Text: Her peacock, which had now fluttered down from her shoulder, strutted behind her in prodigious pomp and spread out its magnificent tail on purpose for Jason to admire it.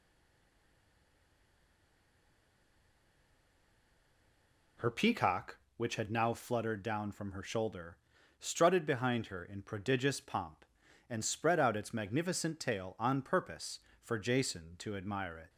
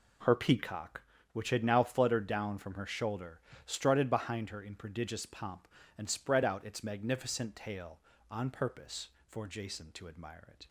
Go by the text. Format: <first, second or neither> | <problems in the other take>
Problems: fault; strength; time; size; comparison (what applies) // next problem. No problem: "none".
second | stays silent before the first word; strong; until 4.7 s; 4.7 s long